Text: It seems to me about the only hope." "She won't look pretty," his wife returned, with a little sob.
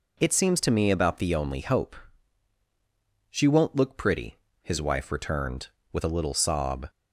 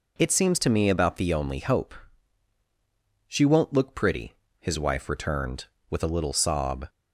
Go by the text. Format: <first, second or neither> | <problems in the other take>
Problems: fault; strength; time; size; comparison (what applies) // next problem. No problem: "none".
neither | none